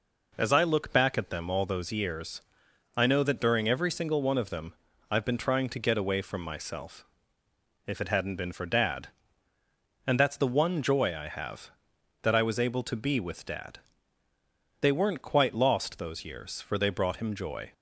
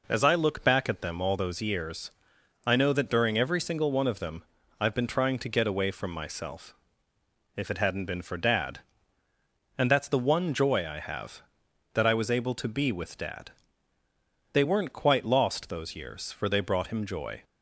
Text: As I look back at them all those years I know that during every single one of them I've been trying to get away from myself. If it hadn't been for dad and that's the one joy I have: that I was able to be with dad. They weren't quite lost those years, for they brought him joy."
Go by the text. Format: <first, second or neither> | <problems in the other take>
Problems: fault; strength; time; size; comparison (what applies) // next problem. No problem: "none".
neither | pauses between "years" and "I"; noticeable; the same in both // pauses between "them" and "I've"; slight; the same in both